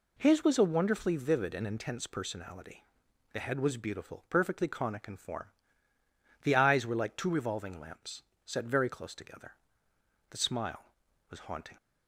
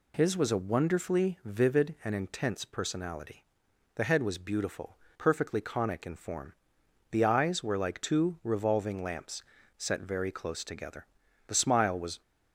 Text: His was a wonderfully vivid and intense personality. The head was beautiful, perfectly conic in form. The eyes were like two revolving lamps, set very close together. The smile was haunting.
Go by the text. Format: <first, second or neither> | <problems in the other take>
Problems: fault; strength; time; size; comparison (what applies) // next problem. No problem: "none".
first | stops before "haunting"; at 12.2 s